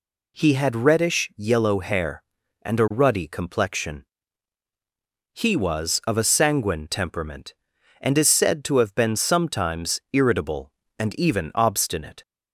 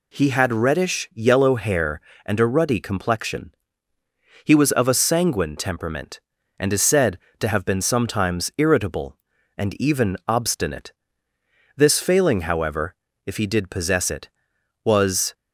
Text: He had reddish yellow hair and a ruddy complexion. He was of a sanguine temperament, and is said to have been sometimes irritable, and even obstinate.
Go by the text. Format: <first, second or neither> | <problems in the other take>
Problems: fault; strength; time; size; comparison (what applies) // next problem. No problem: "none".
first | goes on to say "This failing however if he did possess it was"; strong; from 11.7 s on; 3.5 s long